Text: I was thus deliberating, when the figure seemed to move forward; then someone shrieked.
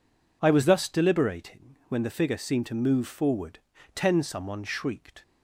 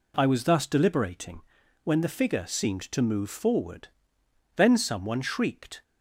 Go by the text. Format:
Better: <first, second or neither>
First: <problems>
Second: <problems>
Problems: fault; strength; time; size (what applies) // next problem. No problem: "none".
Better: second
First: says "ten" for "then"; at 3.9 s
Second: none